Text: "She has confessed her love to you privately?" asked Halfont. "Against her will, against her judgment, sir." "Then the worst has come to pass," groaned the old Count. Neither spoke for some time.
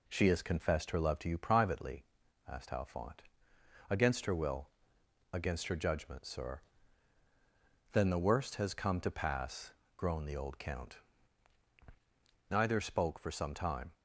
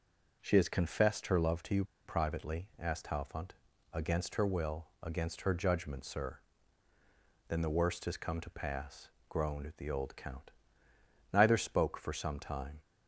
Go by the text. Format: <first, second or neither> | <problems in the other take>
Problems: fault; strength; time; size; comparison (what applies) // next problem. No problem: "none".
first | pauses between "you" and "privately"; slight; at 1.8 s; 0.22 s long